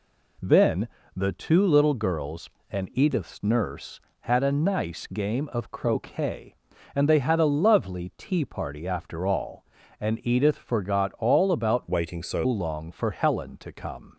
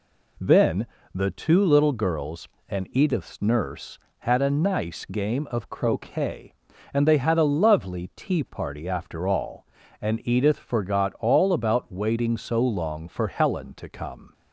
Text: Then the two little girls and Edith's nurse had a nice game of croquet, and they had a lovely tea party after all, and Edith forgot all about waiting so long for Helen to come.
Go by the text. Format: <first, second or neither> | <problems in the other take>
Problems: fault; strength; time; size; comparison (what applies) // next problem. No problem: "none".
second | pauses between "Then" and "the"; slight; at 0.8 s; 0.26 s long; slight in the second // changes voice from "waiting" to "so"; from 11.8 to 12.4 s; 0.6 s long